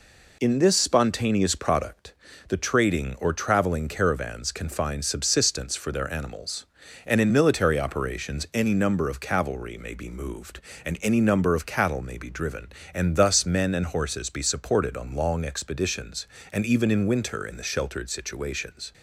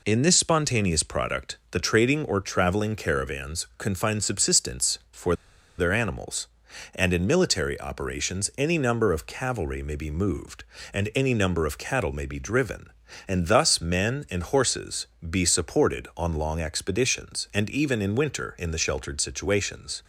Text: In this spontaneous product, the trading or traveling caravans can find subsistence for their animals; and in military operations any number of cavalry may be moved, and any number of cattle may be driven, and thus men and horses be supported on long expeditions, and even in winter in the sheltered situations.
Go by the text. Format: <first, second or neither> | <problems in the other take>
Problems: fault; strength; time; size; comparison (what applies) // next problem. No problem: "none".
first | pauses between "for" and "their"; at 5.3 s; 0.45 s long // pauses between "horses" and "be"; slight; at 15.0 s; 0.20 s long